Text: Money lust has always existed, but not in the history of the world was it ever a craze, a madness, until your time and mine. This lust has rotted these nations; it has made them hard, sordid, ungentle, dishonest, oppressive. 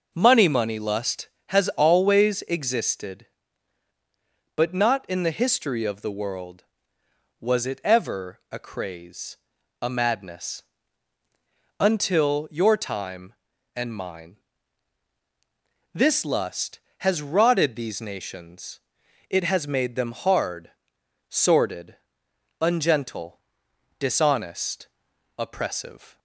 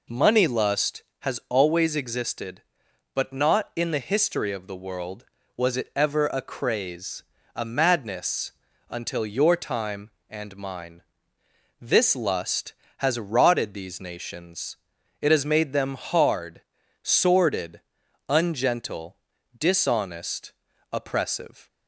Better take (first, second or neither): second